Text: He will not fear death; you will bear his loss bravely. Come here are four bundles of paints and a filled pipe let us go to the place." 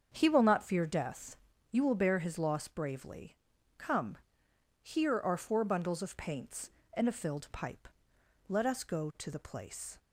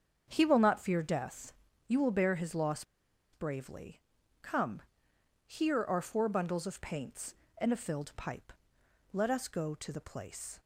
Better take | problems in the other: first | starts louder than the rest; until 1.2 s; 7 dB; also in the first // pauses between "loss" and "bravely"; noticeable; at 2.8 s; 0.49 s long // pauses between "Come" and "here"; noticeable; at 4.8 s; 0.64 s long; noticeable in the first // pauses between "pipe" and "let"; noticeable; at 8.5 s; 0.62 s long; noticeable in the first

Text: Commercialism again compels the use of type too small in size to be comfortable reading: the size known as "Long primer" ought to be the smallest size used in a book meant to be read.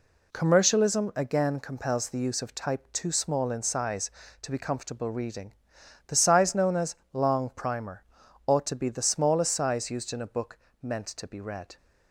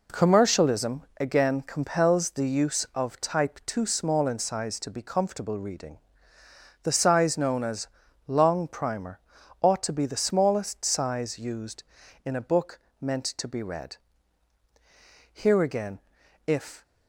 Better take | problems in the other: first | pauses between "Commercialism" and "again"; slight; at 1.0 s; 0.18 s long // pauses between "as" and "Long"; at 7.8 s; 0.40 s long; slight in the first // pauses between "primer" and "ought"; at 9.2 s; 0.40 s long; also in the first // pauses between "book" and "meant"; slight; at 12.8 s; 0.20 s long; slight in the first // goes on to say "Here again if"; from 15.3 s on; 1.5 s long

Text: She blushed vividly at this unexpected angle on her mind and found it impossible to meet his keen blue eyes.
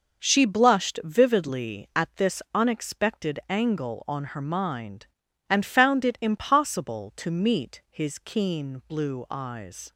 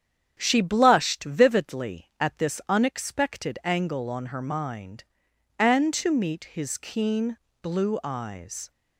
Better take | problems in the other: first | starts louder than the rest; strong; until 1.3 s; 8.5 dB // skips "found it impossible"; at 5.9 s // pauses between "keen" and "blue"; slight; at 7.3 s; 0.24 s long

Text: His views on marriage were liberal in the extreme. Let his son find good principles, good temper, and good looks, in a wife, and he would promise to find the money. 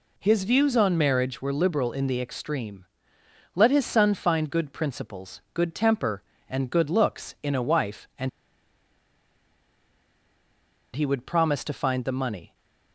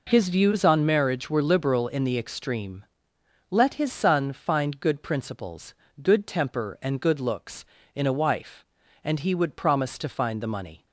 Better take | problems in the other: second | pauses between "and" and "he"; strong; at 8.2 s; 2.6 s long

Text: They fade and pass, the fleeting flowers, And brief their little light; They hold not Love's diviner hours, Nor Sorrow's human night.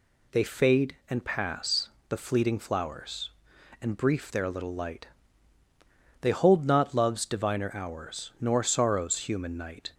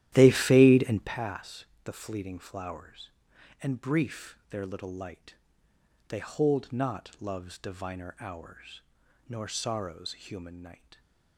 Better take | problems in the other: first | starts louder than the rest; strong; until 1.1 s; 12.5 dB

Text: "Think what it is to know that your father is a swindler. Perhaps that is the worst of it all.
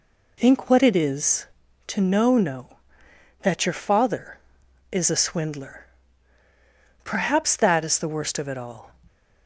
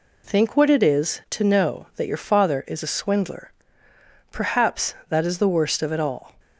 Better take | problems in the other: second | says "know" twice; at 2.3 s

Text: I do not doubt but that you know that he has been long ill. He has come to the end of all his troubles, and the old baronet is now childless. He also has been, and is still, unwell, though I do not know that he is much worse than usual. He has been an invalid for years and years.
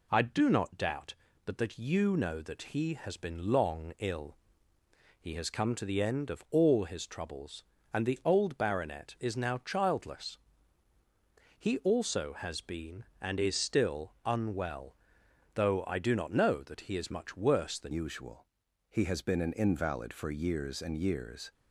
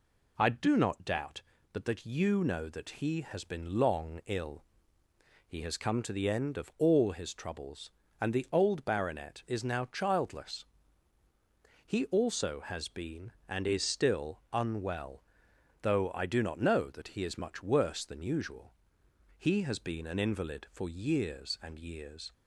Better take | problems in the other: second | changes voice at "usual"; from 17.9 s on; 3.6 s long

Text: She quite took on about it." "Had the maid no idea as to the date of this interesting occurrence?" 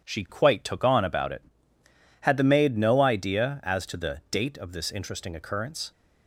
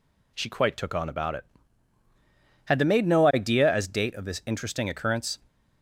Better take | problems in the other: first | skips "to the"; at 3.8 s

